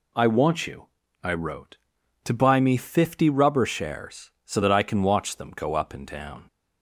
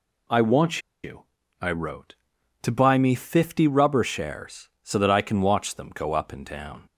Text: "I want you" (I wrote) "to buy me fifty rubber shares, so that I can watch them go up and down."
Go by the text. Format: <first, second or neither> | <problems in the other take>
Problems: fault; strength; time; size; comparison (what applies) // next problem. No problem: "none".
first | pauses between "want" and "you"; slight; at 0.7 s; 0.24 s long